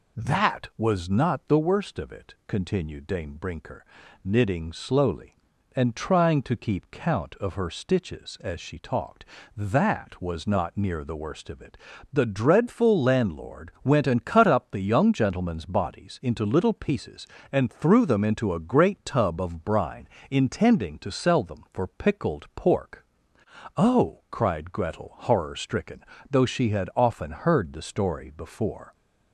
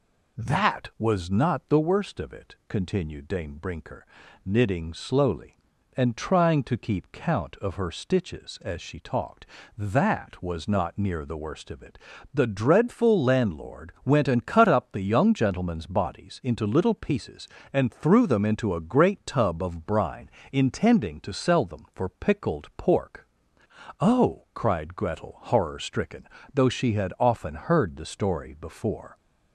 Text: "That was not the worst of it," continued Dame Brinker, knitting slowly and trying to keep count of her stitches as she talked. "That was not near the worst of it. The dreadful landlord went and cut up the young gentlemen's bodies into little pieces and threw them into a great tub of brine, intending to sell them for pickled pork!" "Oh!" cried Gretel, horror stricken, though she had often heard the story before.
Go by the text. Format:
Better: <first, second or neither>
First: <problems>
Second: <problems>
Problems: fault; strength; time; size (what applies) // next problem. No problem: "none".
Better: neither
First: none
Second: none